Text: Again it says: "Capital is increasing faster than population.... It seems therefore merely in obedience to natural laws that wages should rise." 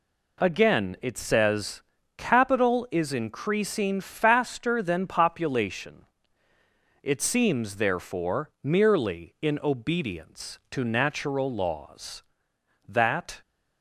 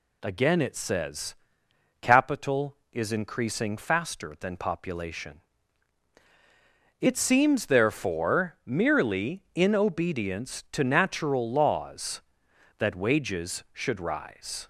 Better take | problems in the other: second | stops before "wages should rise"; at 13.4 s

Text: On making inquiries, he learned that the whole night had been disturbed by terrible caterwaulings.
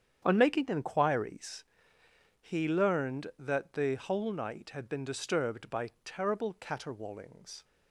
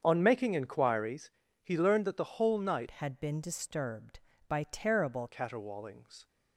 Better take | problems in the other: first | starts louder than the rest; strong; until 1.0 s; 7.5 dB; strong in the first // changes voice from "had" to "terrible"; from 2.9 to 5.2 s; 2.3 s long

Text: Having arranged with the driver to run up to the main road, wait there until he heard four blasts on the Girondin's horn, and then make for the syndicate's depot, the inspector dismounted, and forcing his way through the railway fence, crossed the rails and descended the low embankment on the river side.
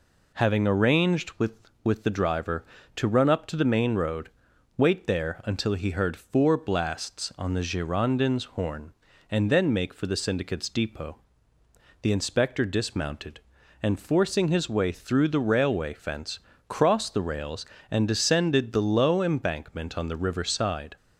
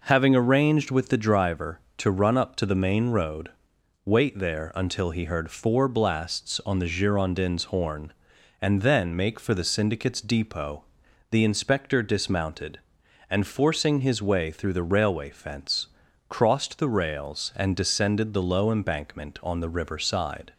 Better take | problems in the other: second | says "with" twice; at 1.8 s

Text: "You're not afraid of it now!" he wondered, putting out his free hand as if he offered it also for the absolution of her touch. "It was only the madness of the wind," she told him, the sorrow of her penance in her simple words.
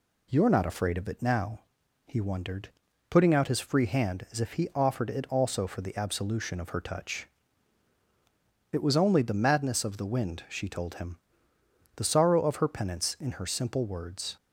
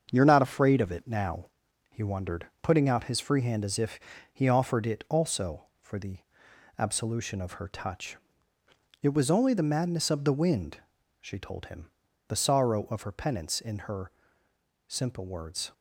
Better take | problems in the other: first | gets quieter; noticeable; throughout; 5.5 dB // pauses between "if" and "he"; slight; at 3.9 s; 0.34 s long // pauses between "the" and "absolution"; noticeable; at 6.2 s; 0.58 s long // pauses between "her" and "simple"; noticeable; at 14.1 s; 0.76 s long

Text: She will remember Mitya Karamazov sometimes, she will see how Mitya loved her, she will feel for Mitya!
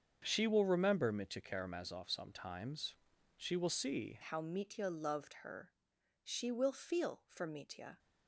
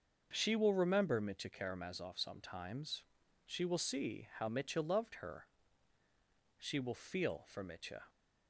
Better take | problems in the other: second | starts louder than the rest; until 1.2 s; 7 dB; also in the second // changes voice at "how"; from 4.2 s on; 3.7 s long

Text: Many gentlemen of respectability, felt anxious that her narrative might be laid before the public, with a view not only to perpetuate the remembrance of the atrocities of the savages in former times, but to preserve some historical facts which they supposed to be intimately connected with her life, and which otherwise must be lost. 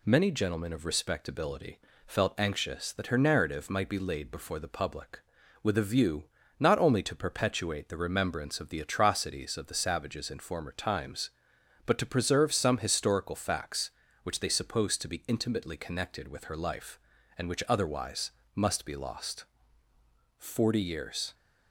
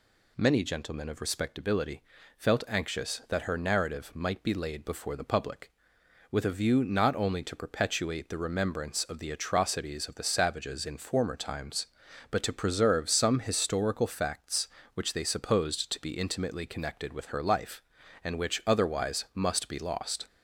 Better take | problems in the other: second | pauses between "view" and "not"; slight; at 6.2 s; 0.36 s long // pauses between "otherwise" and "must"; slight; at 18.3 s; 0.22 s long // goes on to say "Forty years"; noticeable; from 20.3 s on; 0.96 s long

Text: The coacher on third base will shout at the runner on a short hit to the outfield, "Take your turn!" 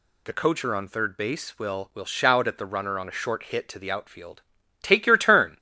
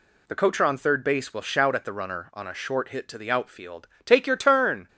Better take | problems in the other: second | says "will" twice; at 1.9 s

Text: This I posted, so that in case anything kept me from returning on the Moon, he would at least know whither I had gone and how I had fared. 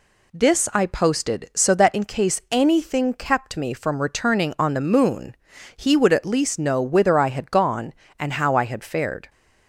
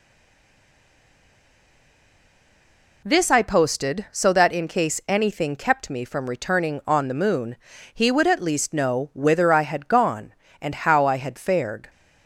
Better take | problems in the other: first | stays silent before the first word; strong; until 3.0 s; 3.0 s long

